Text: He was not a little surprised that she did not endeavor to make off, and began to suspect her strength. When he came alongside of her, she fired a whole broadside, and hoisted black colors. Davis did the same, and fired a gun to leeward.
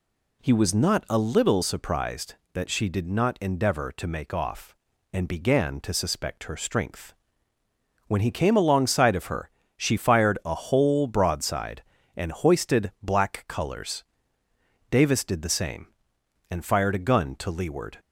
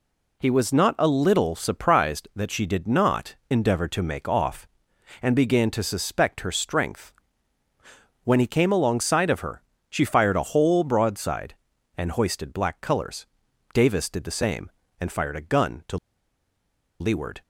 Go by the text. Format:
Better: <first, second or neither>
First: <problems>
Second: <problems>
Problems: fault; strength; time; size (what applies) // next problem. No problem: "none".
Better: first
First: none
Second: pauses between "not" and "endeavor"; slight; at 3.3 s; 0.16 s long // pauses between "to" and "leeward"; at 15.9 s; 1.0 s long